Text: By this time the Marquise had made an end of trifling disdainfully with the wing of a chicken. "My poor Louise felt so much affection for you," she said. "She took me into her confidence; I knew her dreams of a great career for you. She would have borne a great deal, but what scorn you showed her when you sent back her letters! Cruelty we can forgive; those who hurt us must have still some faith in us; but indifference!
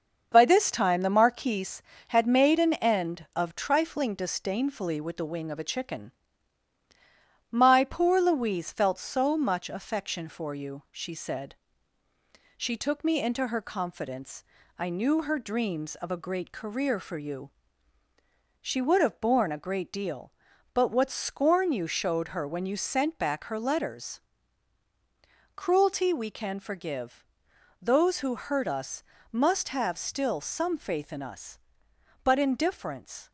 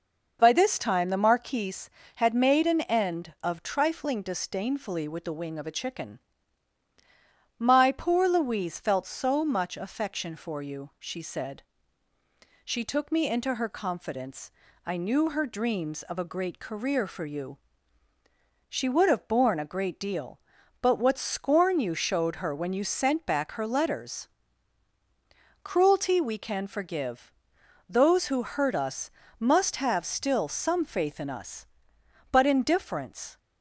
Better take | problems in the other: second | gets quieter; noticeable; throughout; 4 dB // pauses between "us" and "must"; slight; at 29.0 s; 0.32 s long; slight in the second

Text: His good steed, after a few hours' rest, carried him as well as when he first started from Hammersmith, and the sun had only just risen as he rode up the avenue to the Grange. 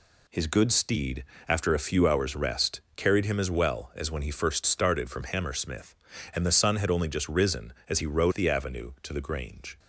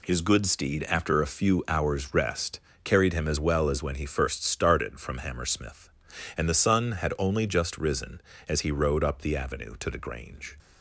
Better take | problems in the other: second | skips "up"; at 8.3 s

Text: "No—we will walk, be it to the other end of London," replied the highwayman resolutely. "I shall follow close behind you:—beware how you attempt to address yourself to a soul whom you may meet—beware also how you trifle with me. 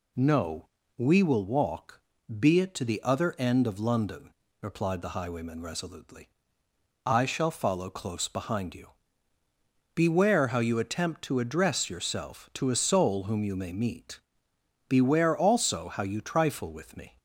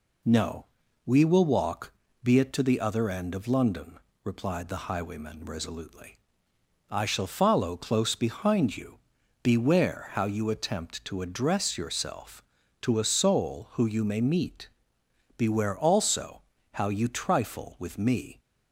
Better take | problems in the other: first | says "who" for "whom"; at 13.7 s // pauses between "also" and "how"; slight; at 16.4 s; 0.34 s long

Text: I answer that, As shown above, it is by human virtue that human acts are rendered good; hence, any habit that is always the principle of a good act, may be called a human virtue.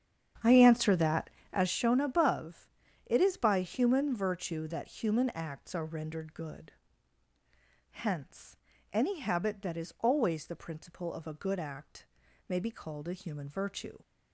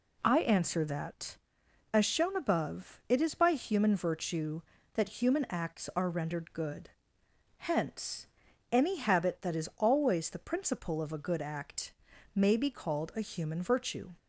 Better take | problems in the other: second | starts louder than the rest; strong; until 1.8 s; 8.5 dB

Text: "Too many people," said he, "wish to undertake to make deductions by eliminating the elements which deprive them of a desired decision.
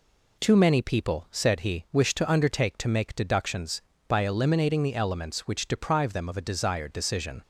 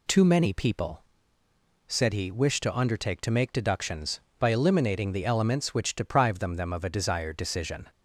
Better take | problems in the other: first | says "them" twice; at 6.5 s

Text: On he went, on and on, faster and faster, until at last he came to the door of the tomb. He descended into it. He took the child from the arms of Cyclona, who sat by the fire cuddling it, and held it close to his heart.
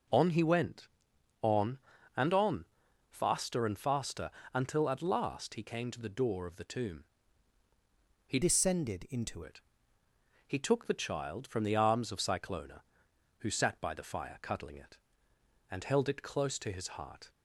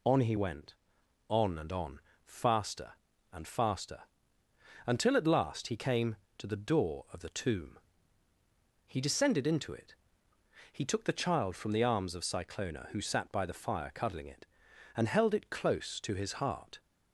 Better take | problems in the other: second | changes voice from "descended" to "into"; from 8.4 to 9.4 s; 1.0 s long

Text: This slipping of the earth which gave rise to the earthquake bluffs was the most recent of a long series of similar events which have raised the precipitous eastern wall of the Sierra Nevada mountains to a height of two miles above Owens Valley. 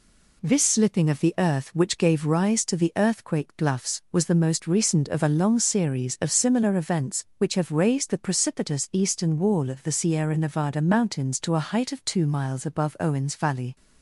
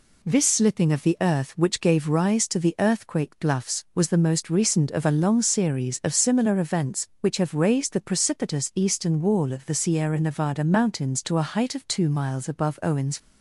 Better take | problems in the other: first | stops before "Valley"; at 13.1 s

